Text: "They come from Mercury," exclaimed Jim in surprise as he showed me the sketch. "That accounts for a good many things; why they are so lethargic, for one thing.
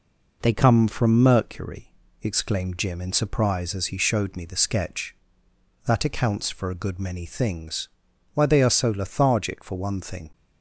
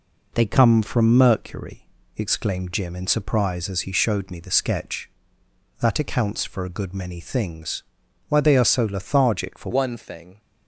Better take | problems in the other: first | changes voice at "one"; from 9.7 s on; 0.6 s long

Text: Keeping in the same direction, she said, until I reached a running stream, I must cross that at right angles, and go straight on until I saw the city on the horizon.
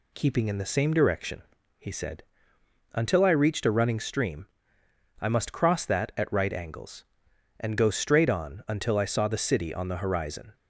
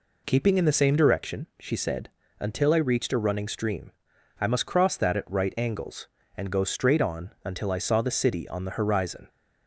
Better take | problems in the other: second | says "he" for "she"; at 1.7 s

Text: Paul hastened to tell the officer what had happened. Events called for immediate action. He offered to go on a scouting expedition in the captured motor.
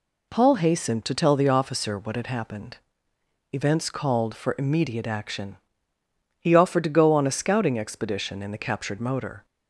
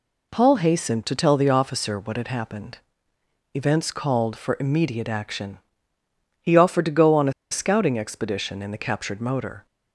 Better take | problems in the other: first | pauses between "a" and "scouting"; slight; at 7.3 s; 0.18 s long

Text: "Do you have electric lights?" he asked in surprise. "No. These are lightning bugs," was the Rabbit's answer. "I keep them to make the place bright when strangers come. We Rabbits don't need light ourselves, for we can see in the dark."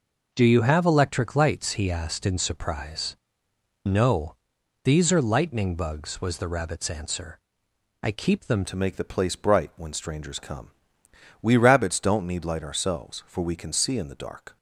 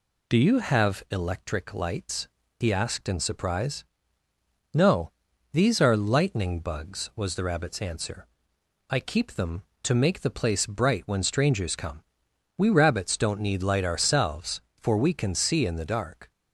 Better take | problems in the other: second | changes voice at "to"; from 8.6 s on; 5.9 s long

